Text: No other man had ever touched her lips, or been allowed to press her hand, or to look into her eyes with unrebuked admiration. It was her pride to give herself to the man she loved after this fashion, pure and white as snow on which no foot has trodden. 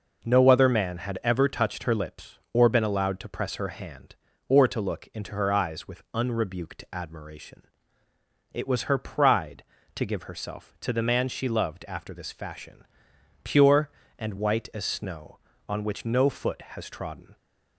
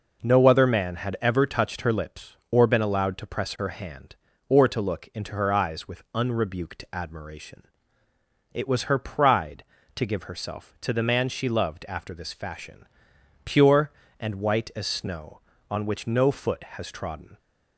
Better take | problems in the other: neither | none

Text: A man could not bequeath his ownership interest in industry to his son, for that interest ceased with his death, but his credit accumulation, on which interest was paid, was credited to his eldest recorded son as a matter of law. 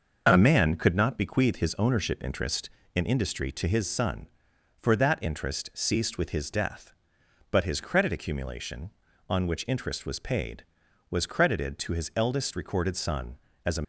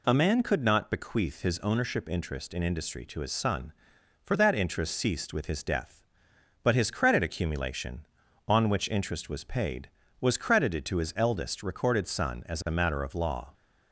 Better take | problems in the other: second | stops before "matter of law"; at 13.8 s

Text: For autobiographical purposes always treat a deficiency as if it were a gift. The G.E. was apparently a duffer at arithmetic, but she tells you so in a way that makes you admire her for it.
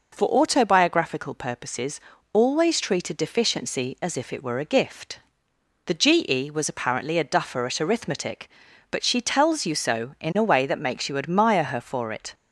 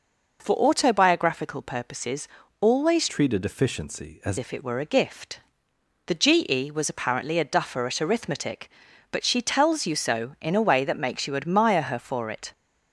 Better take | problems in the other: first | pauses between "purposes" and "always"; slight; at 2.2 s; 0.34 s long; slight in the first // changes voice from "treat" to "as"; from 3.0 to 4.3 s; 1.3 s long

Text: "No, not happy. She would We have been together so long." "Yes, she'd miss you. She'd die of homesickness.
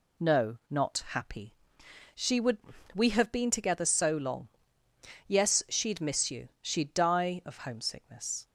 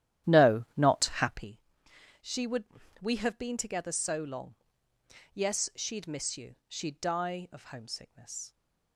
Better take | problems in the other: first | starts louder than the rest; strong; until 1.6 s; 11.5 dB // pauses between "would" and "We"; at 2.6 s; 0.38 s long; also in the first

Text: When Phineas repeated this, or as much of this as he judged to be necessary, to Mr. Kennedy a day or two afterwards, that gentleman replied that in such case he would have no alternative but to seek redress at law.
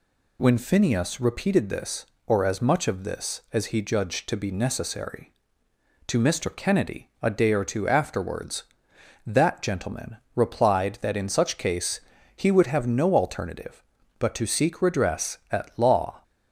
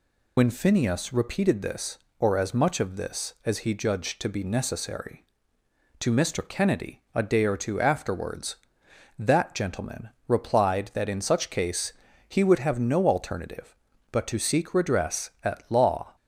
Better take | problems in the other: first | loses the start of "When"; at 0.3 s; 50 ms // pauses between "gentleman" and "replied"; slight; at 10.0 s; 0.18 s long; slight in the first // pauses between "case" and "he"; slight; at 11.9 s; 0.34 s long; slight in the first

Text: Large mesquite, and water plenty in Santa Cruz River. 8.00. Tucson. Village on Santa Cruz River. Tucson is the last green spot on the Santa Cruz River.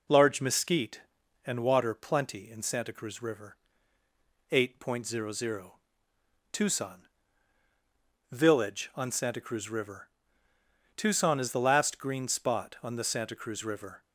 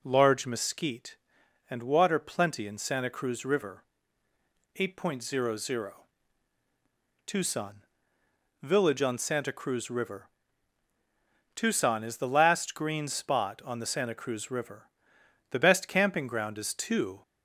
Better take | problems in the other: first | goes on to say "The best camping ground is two"; strong; from 15.4 s on; 1.7 s long

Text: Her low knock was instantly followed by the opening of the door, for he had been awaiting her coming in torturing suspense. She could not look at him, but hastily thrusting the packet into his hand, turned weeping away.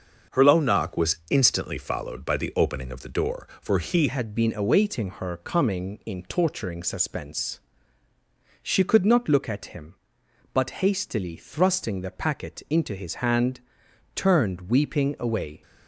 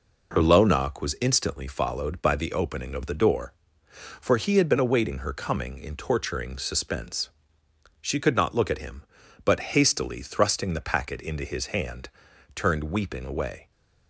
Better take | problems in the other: second | starts louder than the rest; until 1.4 s; 6 dB // changes voice at "had"; from 4.0 s on; 11.6 s long

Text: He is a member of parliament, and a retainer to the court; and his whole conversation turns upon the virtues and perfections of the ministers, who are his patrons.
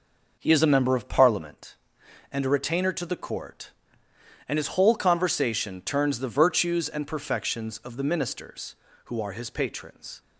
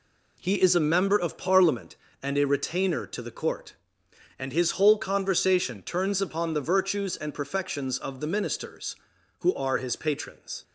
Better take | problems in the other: second | skips "upon"; at 6.2 s

